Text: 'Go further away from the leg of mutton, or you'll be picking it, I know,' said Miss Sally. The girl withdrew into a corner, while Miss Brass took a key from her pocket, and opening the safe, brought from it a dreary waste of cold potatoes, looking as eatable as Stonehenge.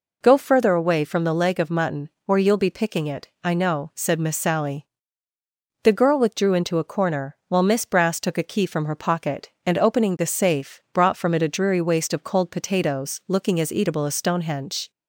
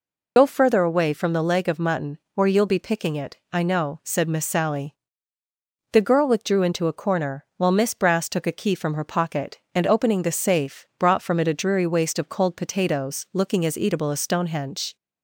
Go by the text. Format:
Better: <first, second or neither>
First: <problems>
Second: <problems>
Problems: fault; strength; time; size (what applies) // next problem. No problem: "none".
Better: first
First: none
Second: loses the start of "Go"; at 0.3 s; 45 ms